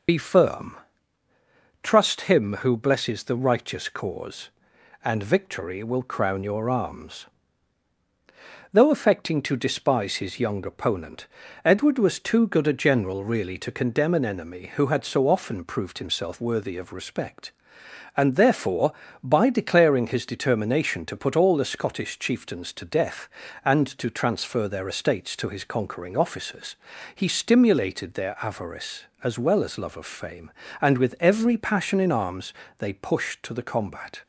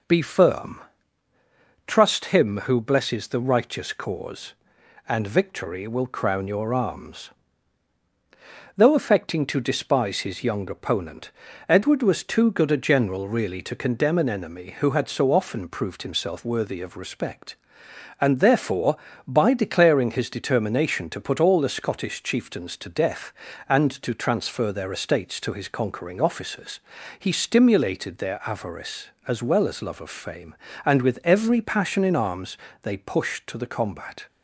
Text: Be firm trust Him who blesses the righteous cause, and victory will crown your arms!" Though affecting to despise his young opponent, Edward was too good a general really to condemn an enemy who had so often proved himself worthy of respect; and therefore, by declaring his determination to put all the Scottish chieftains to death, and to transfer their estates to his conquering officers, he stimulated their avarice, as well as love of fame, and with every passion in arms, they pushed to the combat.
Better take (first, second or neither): second